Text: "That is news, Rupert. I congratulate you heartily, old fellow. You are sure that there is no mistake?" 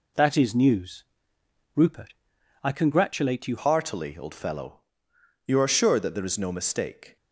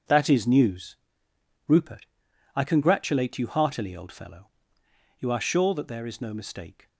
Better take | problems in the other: second | changes voice at "heartily"; from 3.5 s on; 3.6 s long

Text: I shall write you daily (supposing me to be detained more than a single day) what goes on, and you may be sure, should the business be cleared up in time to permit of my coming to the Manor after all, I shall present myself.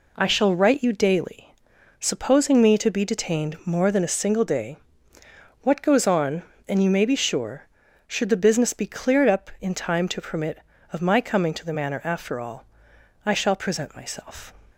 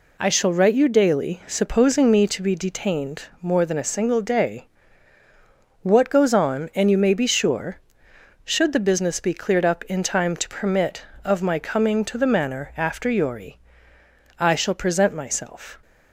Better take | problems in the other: first | pauses between "detained" and "more"; slight; at 3.2 s; 0.18 s long // says "yori" for "all"; at 13.0 s

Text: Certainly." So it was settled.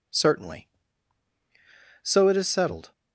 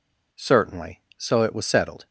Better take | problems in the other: second | says "is" for "was"; at 2.3 s

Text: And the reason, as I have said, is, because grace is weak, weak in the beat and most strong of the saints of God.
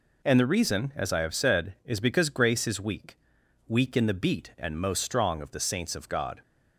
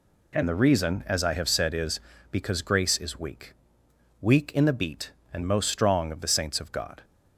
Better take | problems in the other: neither | none

